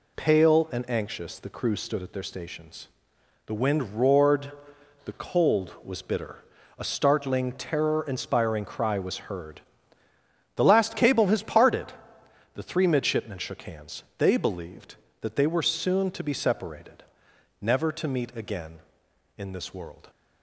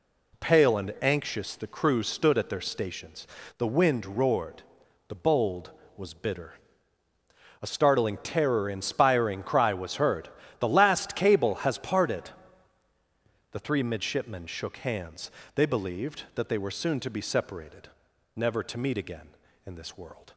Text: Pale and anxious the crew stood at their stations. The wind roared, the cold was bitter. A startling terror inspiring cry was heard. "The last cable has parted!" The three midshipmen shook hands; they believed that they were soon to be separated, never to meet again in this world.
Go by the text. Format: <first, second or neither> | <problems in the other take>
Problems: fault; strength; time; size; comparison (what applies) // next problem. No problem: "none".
first | says "bold" for "cold"; at 5.1 s